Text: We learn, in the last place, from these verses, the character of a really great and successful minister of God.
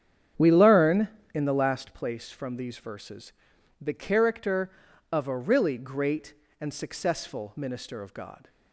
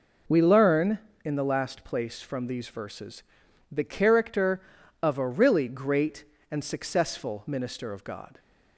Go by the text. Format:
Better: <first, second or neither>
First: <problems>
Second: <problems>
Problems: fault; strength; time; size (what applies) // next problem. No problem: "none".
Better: second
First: starts louder than the rest; strong; until 2.0 s; 8.5 dB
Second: none